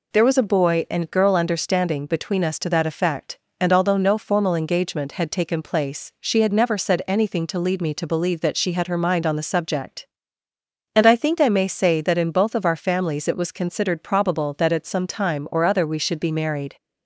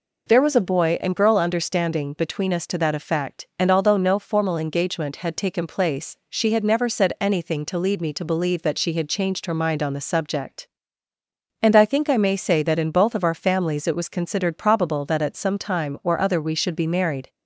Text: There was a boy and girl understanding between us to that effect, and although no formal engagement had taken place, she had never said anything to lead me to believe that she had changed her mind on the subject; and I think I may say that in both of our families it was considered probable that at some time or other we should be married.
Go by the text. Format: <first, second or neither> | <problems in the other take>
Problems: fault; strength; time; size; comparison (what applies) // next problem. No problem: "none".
second | skips "changed"; at 8.8 s